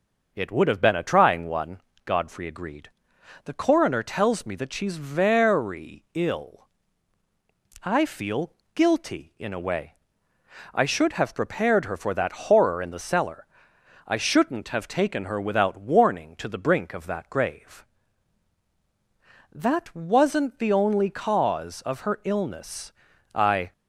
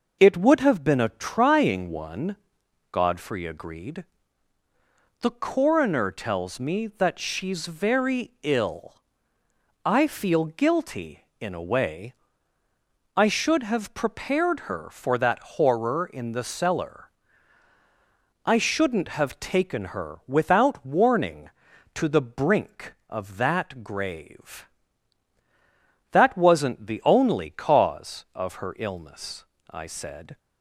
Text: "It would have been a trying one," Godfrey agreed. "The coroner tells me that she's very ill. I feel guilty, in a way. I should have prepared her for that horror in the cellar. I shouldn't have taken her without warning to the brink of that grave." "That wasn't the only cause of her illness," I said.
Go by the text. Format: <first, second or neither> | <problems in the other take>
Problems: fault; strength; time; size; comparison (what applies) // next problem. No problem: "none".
second | pauses between "feel" and "guilty"; slight; at 8.5 s; 0.22 s long // stops before "said"; at 23.7 s